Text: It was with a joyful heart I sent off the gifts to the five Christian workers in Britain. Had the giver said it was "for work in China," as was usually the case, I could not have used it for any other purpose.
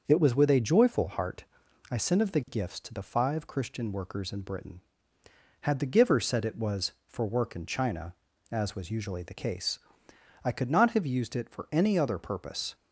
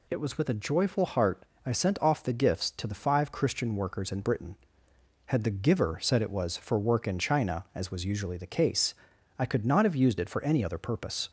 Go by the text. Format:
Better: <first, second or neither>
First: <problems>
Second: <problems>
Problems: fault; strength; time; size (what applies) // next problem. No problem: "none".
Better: second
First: starts louder than the rest; until 1.0 s; 6 dB // pauses between "heart" and "I"; at 1.4 s; 0.44 s long // says "of" for "off"; at 2.2 s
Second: pauses between "heart" and "I"; slight; at 1.4 s; 0.22 s long